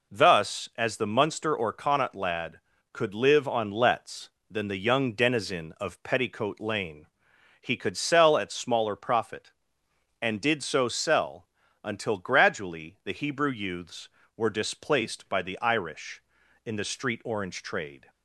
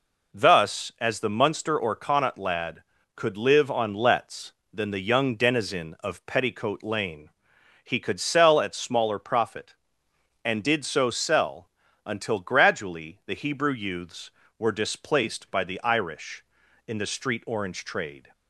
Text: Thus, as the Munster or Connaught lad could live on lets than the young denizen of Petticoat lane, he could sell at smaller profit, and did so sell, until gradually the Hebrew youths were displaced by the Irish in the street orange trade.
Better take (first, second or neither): neither